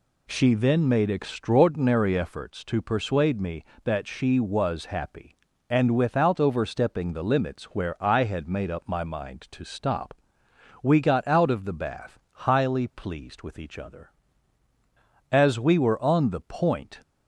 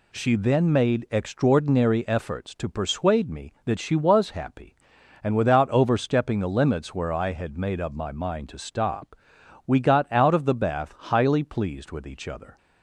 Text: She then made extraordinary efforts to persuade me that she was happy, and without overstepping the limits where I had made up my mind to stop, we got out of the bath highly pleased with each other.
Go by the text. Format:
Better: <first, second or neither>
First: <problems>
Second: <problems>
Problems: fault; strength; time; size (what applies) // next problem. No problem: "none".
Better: second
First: goes on to say "As we were on the point"; strong; from 15.3 s on; 1.7 s long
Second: none